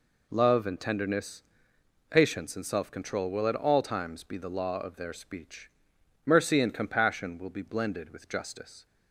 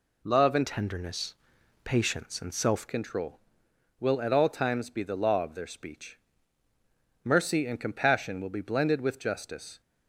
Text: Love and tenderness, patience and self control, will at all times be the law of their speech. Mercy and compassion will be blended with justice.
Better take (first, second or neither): first